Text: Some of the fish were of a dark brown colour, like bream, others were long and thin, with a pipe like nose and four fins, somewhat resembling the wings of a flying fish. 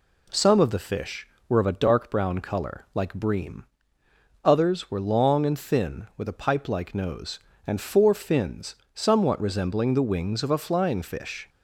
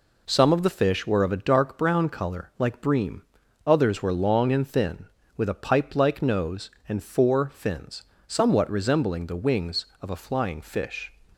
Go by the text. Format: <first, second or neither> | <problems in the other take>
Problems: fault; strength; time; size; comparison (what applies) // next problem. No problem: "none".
neither | none